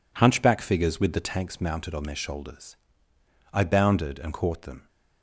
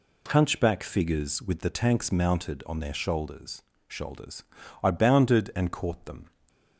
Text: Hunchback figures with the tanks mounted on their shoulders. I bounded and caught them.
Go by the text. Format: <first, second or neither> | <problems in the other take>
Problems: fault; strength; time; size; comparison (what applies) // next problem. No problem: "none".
first | says "shoulders" twice; at 3.8 s // stays silent after the last word; slight; from 6.2 s on; 0.5 s long